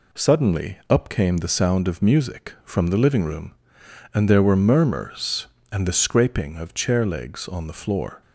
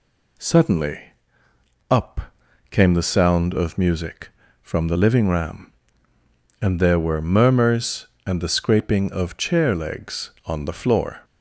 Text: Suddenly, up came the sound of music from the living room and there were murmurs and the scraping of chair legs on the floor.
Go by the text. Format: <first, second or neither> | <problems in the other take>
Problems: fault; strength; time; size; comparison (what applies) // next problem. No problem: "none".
first | pauses between "up" and "came"; noticeable; at 2.2 s; 0.48 s long // says "ram" for "room"; at 5.2 s